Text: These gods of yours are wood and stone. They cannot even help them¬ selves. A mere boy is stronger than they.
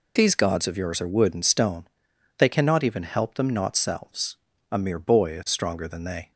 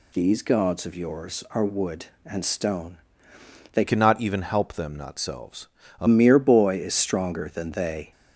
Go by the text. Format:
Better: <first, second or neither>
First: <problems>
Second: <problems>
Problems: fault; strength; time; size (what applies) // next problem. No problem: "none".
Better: first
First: none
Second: changes voice from "cannot" to "A"; from 3.8 to 6.0 s; 2.2 s long